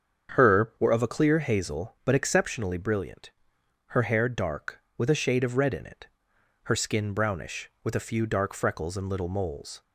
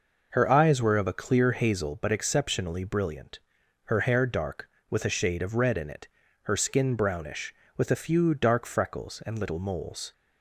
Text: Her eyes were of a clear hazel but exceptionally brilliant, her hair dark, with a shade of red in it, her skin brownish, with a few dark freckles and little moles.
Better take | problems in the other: second | starts louder than the rest; strong; until 1.3 s; 7.5 dB // skips "eyes"; at 0.7 s

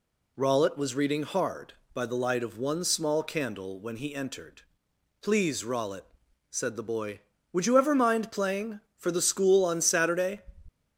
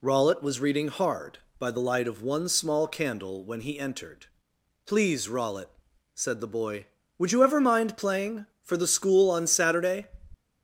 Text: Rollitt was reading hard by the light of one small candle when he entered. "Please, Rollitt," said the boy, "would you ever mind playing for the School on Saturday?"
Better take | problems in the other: neither | none

